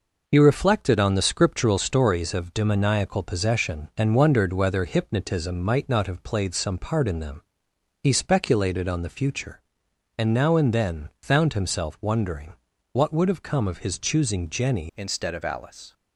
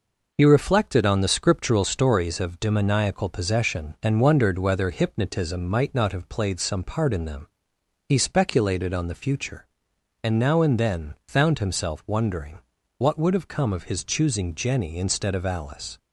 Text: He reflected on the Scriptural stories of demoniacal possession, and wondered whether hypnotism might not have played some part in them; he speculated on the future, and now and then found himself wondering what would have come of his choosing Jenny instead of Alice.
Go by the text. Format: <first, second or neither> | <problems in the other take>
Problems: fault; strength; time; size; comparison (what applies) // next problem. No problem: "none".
second | pauses between "wondering" and "what"; at 12.5 s; 0.38 s long; also in the second // changes voice at "instead"; from 14.9 s on; 1.0 s long